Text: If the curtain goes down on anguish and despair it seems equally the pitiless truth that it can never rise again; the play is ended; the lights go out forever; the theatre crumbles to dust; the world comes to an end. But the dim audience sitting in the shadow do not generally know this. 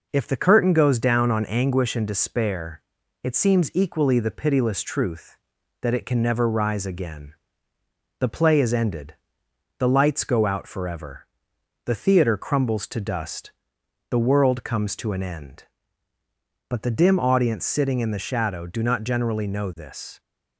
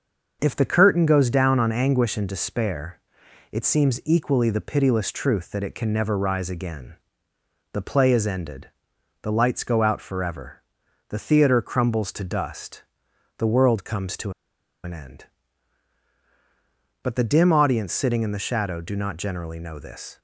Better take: first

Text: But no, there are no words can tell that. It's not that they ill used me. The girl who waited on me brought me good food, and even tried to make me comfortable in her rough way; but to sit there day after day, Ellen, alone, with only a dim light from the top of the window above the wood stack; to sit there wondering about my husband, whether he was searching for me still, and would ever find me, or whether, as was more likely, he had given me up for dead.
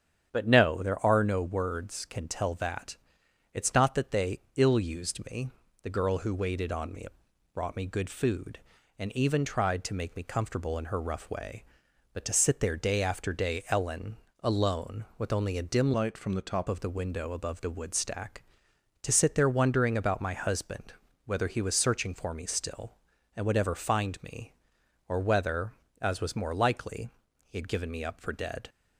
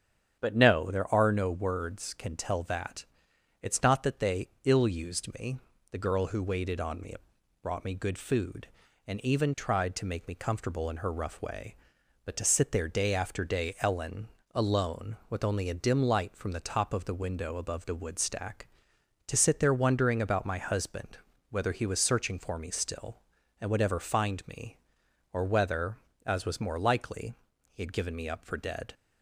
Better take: second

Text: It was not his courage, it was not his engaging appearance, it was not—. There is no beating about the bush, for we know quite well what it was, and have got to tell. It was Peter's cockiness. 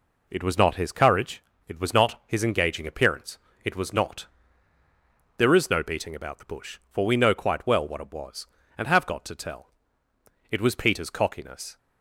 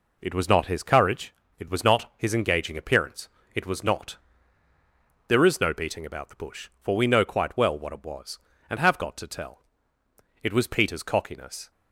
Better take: neither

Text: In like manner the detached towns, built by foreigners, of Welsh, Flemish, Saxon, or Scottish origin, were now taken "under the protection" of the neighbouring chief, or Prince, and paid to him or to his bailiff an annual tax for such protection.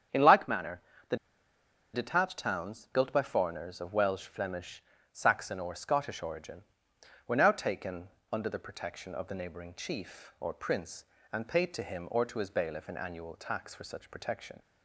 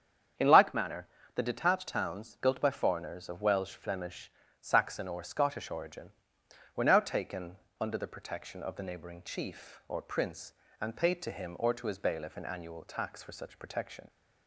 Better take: second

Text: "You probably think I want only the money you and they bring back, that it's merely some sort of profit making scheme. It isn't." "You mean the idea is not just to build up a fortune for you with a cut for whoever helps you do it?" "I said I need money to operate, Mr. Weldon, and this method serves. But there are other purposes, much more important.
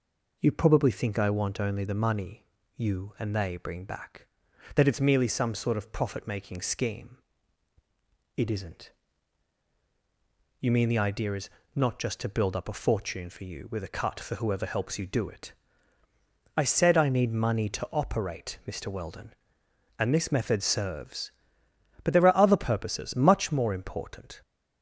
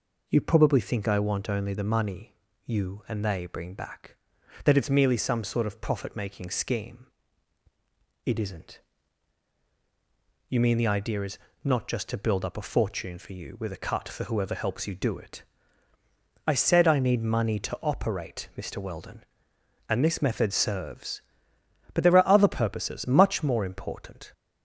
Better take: neither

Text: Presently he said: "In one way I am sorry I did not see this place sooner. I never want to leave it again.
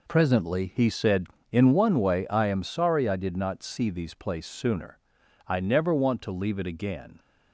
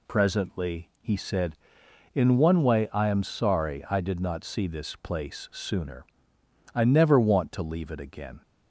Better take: second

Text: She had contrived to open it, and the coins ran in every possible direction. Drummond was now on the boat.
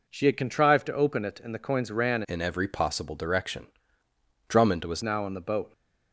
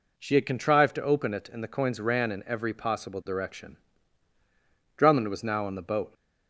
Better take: second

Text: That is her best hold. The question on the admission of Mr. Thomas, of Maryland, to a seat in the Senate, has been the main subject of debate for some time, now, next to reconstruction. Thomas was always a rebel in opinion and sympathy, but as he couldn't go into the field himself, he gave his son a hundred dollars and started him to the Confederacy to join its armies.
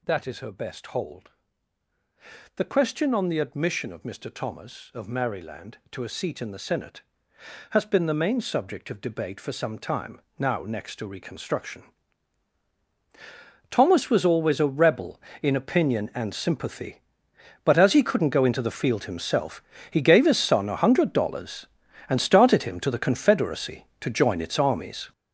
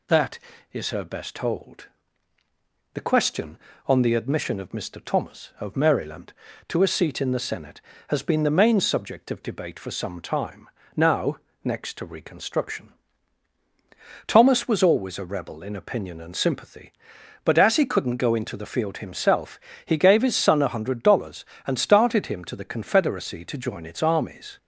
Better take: second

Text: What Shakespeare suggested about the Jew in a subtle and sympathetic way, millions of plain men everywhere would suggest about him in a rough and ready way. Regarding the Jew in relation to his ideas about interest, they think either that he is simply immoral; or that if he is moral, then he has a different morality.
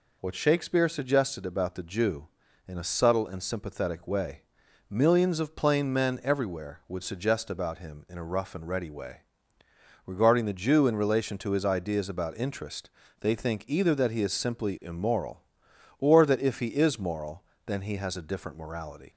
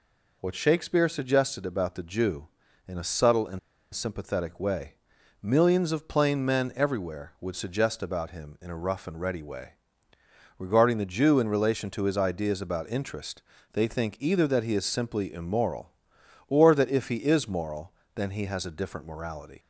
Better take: first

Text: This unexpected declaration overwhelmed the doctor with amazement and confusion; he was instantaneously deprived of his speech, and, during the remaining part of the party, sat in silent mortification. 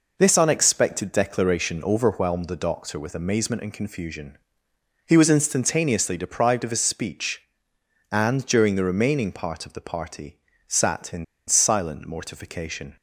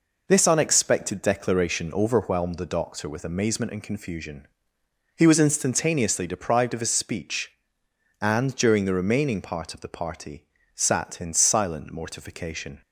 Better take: second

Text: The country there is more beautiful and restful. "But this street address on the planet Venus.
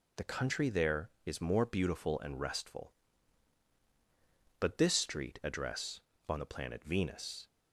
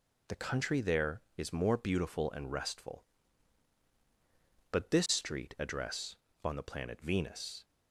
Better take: neither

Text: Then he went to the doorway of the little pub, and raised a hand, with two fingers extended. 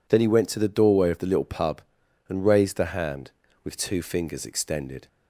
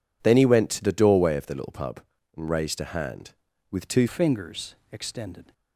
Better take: first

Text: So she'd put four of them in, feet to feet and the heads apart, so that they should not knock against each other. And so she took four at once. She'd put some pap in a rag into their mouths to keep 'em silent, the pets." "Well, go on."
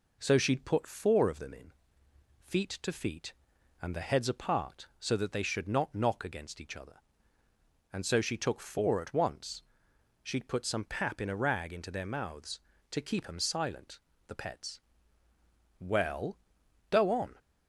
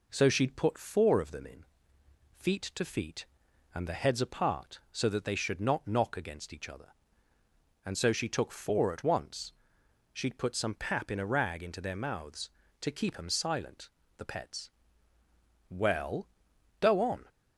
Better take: neither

